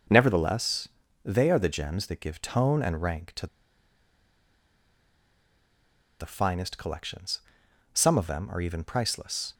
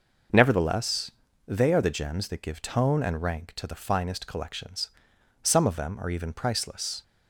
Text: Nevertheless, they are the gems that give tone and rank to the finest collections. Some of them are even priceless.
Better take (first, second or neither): second